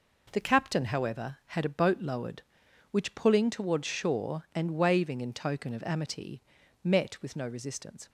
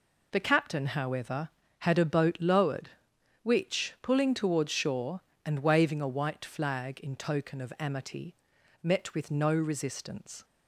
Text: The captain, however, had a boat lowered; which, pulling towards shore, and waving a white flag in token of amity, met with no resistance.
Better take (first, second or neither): second